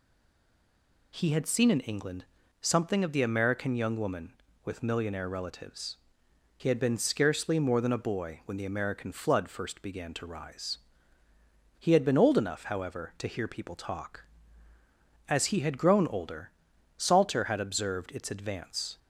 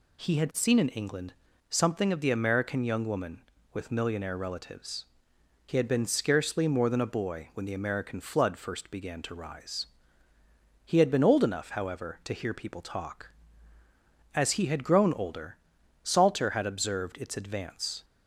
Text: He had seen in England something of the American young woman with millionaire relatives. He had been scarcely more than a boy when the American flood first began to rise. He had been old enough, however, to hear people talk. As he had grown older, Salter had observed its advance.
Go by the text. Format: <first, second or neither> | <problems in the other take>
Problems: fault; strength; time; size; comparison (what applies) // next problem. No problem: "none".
second | stays silent before the first word; until 1.1 s; 1.1 s long // pauses between "England" and "something"; slight; at 2.2 s; 0.36 s long; slight in the second